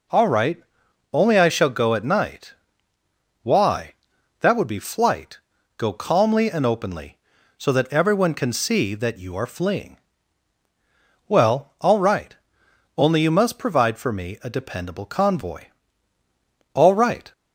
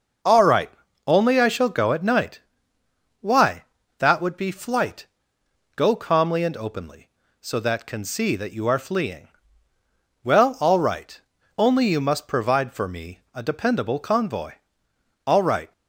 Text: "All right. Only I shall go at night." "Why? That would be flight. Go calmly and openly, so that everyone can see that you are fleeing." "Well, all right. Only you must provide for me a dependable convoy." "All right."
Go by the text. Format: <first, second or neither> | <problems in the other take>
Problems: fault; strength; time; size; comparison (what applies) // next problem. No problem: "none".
first | skips "everyone"; at 7.8 s